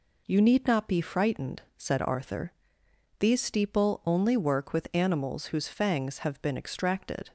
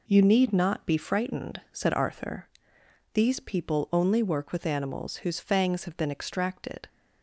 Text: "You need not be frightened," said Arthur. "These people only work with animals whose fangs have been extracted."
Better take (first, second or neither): second